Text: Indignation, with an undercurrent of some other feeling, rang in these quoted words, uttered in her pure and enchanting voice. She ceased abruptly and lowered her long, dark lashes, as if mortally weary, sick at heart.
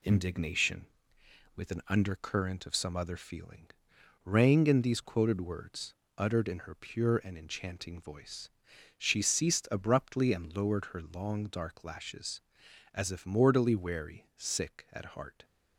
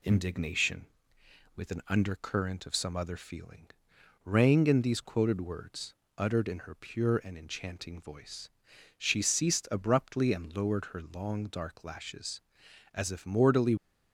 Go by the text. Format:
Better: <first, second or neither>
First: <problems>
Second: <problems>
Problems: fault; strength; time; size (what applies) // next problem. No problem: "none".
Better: first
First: none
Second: stops before "weary sick at heart"; at 13.7 s